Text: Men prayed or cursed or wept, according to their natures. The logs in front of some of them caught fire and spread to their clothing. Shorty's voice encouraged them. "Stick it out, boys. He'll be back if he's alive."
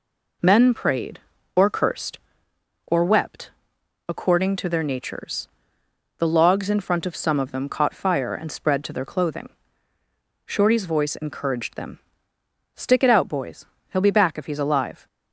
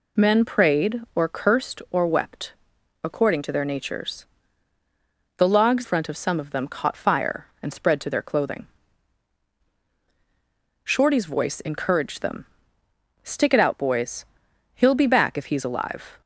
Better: first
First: none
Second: skips "in"; at 5.8 s

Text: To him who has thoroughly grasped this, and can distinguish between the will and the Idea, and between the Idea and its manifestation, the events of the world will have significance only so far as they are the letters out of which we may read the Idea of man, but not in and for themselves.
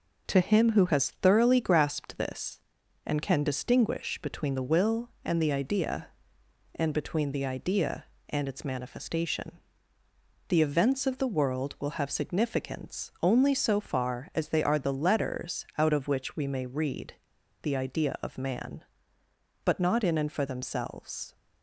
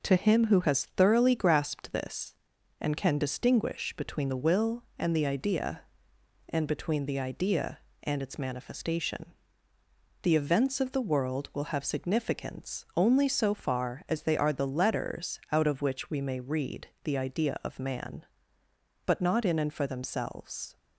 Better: second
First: pauses between "read" and "the"; noticeable; at 17.1 s; 0.46 s long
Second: none

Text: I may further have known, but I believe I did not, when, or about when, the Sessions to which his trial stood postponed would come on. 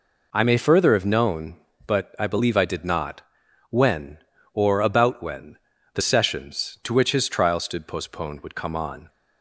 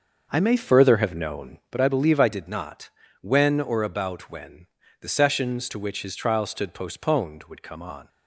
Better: first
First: none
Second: starts louder than the rest; noticeable; until 1.7 s; 6 dB

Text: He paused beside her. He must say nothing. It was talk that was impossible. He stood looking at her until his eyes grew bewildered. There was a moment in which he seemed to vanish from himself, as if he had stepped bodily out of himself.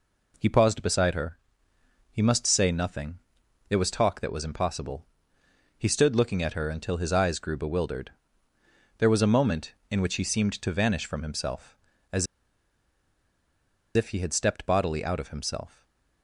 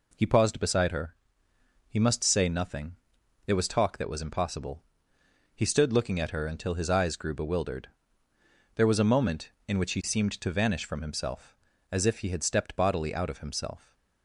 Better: second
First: pauses between "as" and "if"; strong; at 12.2 s; 1.7 s long // stays silent after the last word; slight; from 15.6 s on; 0.6 s long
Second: none

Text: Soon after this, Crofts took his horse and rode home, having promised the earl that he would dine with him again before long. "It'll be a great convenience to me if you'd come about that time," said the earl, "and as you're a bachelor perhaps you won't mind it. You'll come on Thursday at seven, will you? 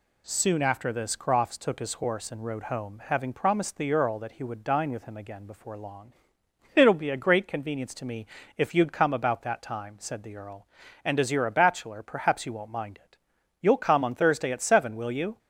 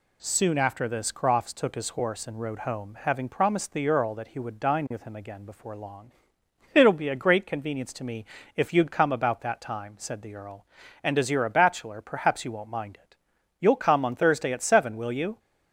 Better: neither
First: pauses between "me" and "if"; slight; at 8.2 s; 0.30 s long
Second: pauses between "me" and "if"; slight; at 8.2 s; 0.30 s long

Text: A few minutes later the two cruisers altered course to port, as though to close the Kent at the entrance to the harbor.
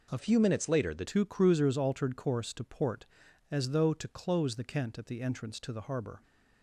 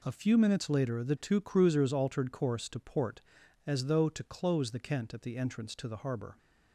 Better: second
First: changes voice from "few" to "the"; from 0.1 to 1.0 s; 0.9 s long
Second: none

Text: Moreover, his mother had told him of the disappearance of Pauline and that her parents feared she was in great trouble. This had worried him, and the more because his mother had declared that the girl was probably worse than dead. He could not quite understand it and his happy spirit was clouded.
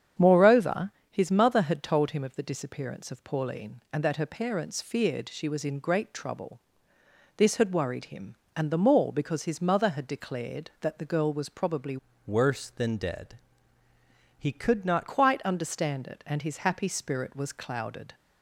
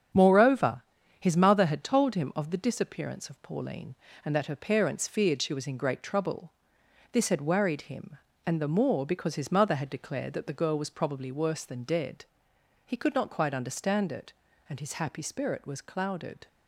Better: second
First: starts louder than the rest; strong; until 1.3 s; 8.5 dB // changes voice from "worse" to "not"; from 12.2 to 15.0 s; 2.8 s long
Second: starts louder than the rest; strong; until 1.5 s; 8 dB

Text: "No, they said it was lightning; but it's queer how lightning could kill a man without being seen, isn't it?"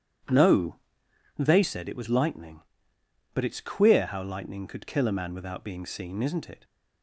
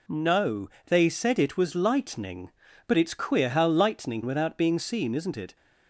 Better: first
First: none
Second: skips "could kill a man"; at 4.2 s

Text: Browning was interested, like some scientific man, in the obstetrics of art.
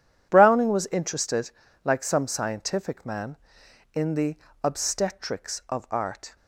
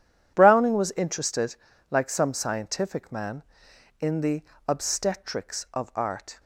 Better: neither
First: pauses between "the" and "obstetrics"; slight; at 4.3 s; 0.26 s long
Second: pauses between "the" and "obstetrics"; slight; at 4.4 s; 0.24 s long

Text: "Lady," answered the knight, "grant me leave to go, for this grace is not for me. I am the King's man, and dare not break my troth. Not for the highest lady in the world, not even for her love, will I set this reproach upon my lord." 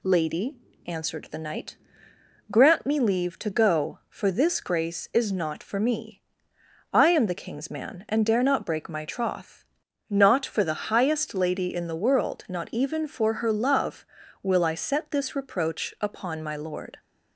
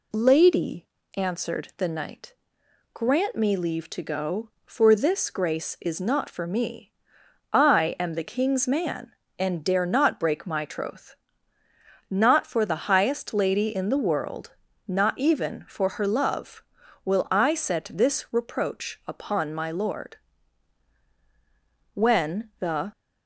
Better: first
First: none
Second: goes on to say "When the"; noticeable; from 21.9 s on; 0.98 s long

